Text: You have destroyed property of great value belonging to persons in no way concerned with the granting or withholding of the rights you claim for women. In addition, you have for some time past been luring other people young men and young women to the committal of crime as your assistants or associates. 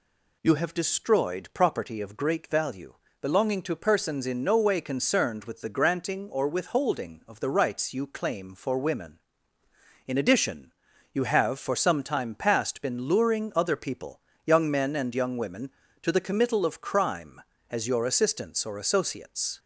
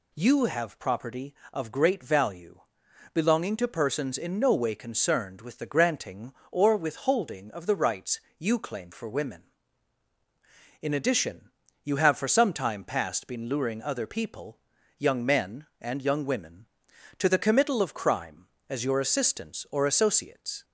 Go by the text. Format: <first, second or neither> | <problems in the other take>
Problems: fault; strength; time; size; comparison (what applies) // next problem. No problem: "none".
first | skips "destroyed"; at 0.7 s // pauses between "value" and "belonging"; noticeable; at 2.6 s; 0.52 s long; slight in the first // pauses between "rights" and "you"; slight; at 8.2 s; 0.18 s long // pauses between "people" and "young"; at 14.5 s; 0.40 s long; slight in the first